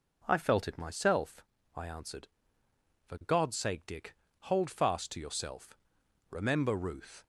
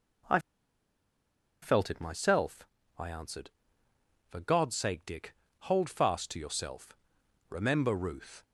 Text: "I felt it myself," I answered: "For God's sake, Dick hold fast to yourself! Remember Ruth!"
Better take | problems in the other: first | pauses between "I" and "felt"; at 0.3 s; 1.2 s long // pauses between "Dick" and "hold"; slight; at 5.3 s; 0.24 s long; slight in the first

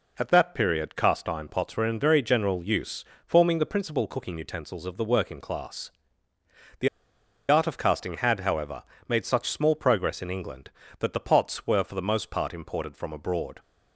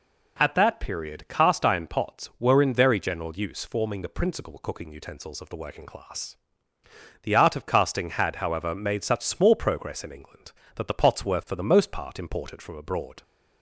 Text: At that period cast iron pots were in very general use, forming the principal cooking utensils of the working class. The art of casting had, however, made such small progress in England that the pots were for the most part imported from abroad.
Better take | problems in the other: second | pauses between "The" and "art"; noticeable; at 6.8 s; 0.61 s long

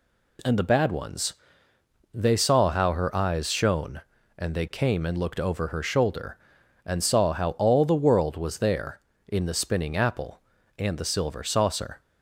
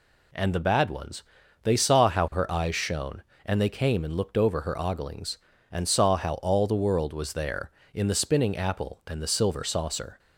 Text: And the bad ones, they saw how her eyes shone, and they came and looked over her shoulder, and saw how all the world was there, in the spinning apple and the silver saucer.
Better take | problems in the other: first | says "oglings" for "shoulder"; at 4.7 s

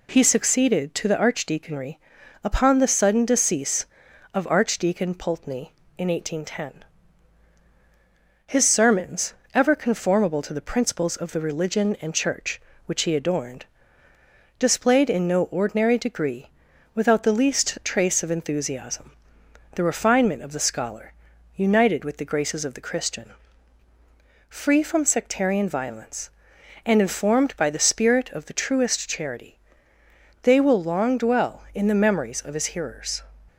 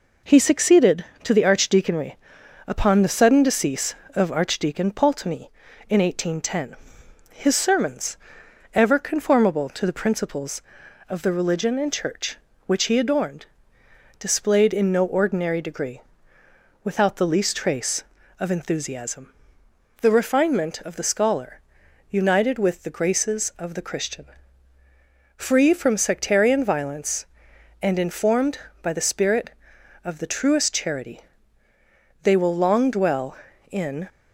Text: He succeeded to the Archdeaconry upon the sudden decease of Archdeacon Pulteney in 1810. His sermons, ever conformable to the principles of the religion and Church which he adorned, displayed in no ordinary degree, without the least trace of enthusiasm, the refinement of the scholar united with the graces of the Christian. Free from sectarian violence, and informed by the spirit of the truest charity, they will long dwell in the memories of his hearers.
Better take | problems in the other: first | pauses between "Archdeaconry" and "upon"; noticeable; at 2.1 s; 0.50 s long; also in the first // pauses between "scholar" and "united"; noticeable; at 21.6 s; 0.48 s long; also in the first // stops before "the memories of his hearers"; at 34.0 s

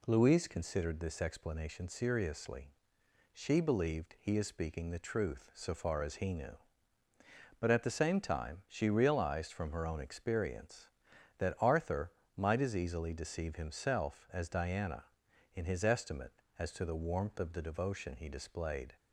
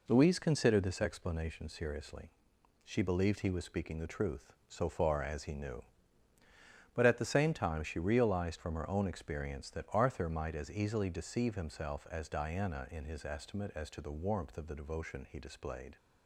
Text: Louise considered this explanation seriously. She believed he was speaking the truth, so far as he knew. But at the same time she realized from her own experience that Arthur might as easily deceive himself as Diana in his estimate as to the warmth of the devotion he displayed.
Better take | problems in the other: second | says "is" for "was"; at 4.3 s // pauses between "Arthur" and "might"; slight; at 12.1 s; 0.24 s long

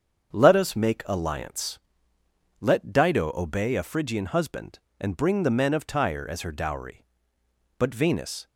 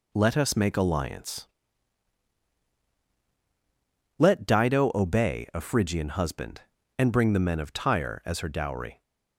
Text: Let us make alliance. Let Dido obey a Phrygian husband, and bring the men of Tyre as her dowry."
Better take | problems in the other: second | starts louder than the rest; strong; until 1.3 s; 7 dB // goes on to say "But Venus"; noticeable; from 7.7 s on; 0.68 s long

